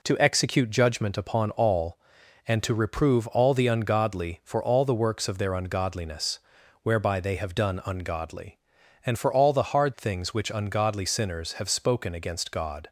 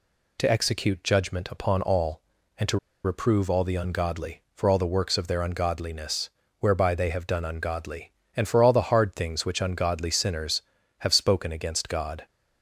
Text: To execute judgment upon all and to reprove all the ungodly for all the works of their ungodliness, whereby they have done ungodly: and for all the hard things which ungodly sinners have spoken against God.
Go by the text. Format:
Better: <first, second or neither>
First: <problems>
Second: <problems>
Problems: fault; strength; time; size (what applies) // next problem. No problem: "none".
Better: first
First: none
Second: pauses between "to" and "reprove"; slight; at 2.7 s; 0.26 s long